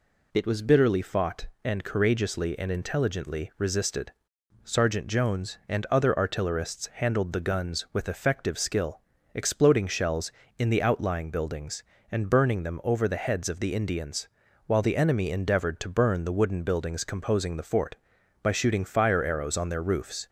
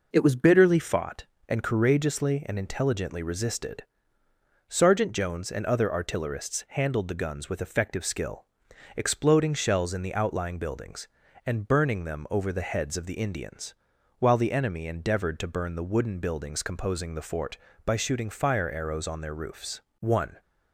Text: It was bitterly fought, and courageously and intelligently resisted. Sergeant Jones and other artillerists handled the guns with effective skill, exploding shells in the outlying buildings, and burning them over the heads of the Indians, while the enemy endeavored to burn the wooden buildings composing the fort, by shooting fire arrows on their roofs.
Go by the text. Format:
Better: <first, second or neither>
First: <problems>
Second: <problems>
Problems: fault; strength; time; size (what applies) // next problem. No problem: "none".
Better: first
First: none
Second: goes on to say "One"; slight; from 20.0 s on; 0.40 s long